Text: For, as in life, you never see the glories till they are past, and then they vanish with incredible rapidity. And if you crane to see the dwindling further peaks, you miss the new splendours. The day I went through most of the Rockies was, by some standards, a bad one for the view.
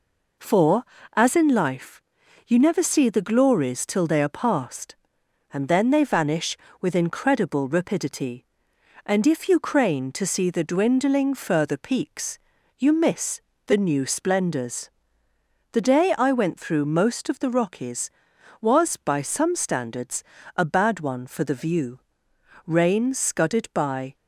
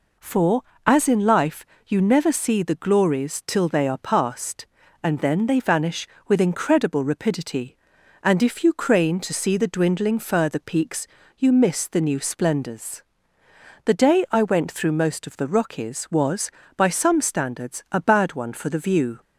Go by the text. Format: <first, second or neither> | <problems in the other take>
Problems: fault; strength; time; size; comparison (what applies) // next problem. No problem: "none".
second | pauses between "miss" and "the"; slight; at 13.4 s; 0.26 s long // goes on to say "Rain scudded by"; from 22.6 s on; 1.4 s long